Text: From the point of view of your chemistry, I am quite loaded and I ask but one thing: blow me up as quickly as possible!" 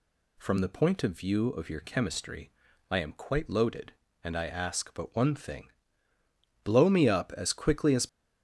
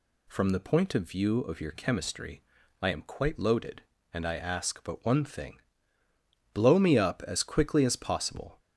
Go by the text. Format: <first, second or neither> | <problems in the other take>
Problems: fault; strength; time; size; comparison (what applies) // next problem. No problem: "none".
second | stops before "possible"; at 8.0 s